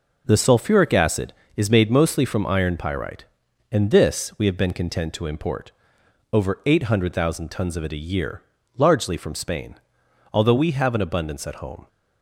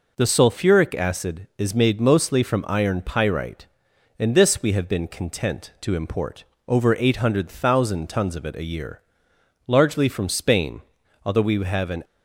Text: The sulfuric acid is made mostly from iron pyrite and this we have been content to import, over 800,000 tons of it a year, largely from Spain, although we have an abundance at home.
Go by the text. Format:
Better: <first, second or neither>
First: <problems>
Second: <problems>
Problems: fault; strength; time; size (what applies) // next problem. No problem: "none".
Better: first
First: none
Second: stops before "abundance at home"; at 12.0 s